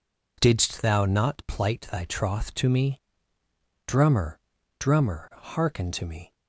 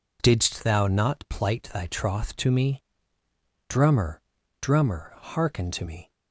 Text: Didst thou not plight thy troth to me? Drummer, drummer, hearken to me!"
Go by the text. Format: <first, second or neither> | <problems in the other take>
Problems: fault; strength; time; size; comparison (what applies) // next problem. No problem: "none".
neither | none